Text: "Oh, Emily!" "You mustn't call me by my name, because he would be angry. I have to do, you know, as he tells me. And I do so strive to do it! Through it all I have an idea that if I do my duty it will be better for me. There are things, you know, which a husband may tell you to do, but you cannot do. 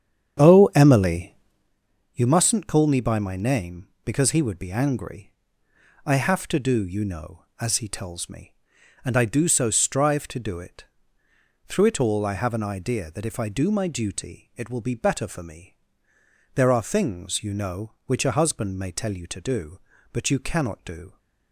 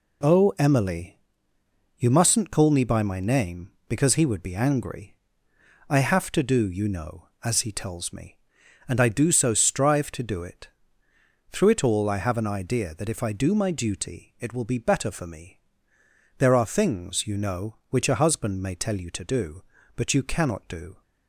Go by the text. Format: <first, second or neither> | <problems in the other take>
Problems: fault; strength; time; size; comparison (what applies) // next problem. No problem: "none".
second | starts louder than the rest; strong; until 1.7 s; 8.5 dB